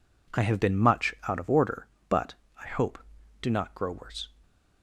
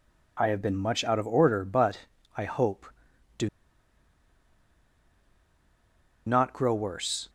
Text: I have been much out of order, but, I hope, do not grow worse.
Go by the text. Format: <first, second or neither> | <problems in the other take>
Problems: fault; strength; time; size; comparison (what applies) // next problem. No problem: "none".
first | pauses between "do" and "not"; strong; at 3.4 s; 2.7 s long